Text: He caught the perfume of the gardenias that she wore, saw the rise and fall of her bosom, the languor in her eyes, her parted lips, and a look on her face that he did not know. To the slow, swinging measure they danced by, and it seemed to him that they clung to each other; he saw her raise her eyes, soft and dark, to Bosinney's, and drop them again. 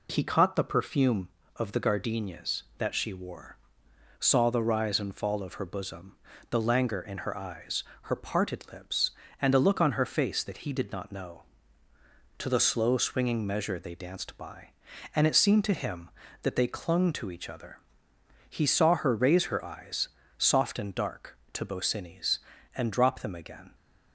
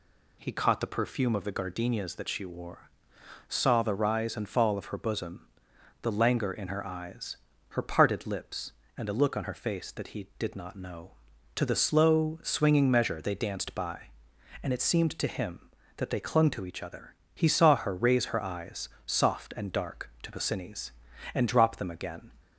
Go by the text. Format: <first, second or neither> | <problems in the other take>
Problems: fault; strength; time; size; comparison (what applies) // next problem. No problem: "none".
neither | none